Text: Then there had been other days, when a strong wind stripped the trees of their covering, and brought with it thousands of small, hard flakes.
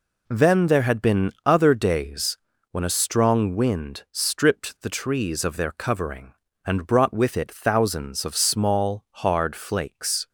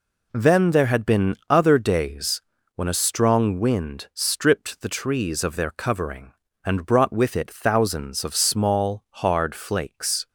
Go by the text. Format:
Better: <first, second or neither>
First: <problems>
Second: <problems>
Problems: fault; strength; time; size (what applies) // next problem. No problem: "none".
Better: neither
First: none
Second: none